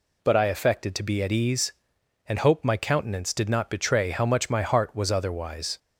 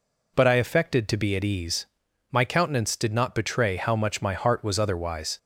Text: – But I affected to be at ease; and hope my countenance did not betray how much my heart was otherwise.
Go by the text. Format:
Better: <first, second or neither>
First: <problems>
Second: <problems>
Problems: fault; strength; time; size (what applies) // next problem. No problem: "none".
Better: first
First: none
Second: skips "and hope"; at 2.0 s